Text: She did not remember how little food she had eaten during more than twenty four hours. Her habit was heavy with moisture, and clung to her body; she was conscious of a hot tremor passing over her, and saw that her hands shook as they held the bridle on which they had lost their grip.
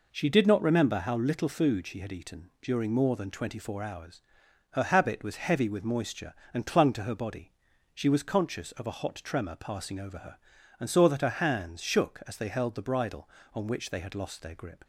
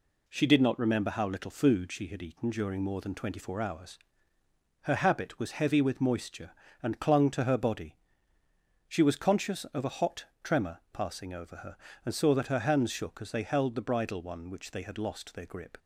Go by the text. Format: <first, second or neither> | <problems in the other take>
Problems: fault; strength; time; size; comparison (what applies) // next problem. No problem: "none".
first | pauses between "hot" and "tremor"; slight; at 10.2 s; 0.18 s long // says "one" for "on"; at 14.2 s